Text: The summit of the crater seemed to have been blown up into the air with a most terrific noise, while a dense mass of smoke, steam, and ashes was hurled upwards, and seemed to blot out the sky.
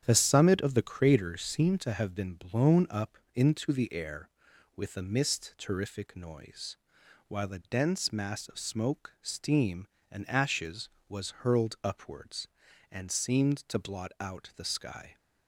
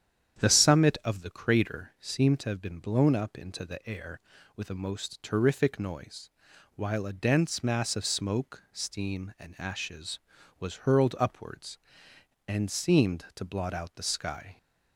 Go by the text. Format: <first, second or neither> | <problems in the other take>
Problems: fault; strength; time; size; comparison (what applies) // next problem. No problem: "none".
second | starts louder than the rest; strong; until 1.0 s; 9 dB; strong in the second // pauses between "up" and "into"; slight; at 3.1 s; 0.18 s long // says "mist" for "most"; at 5.0 s